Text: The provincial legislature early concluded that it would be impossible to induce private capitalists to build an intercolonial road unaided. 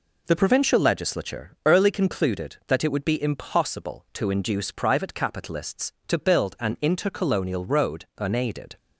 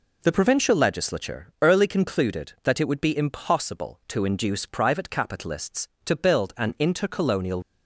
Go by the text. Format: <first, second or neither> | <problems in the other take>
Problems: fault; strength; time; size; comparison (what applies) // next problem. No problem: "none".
first | pauses between "legislature" and "early"; slight; at 1.4 s; 0.16 s long; slight in the first // stops before "road unaided"; at 7.6 s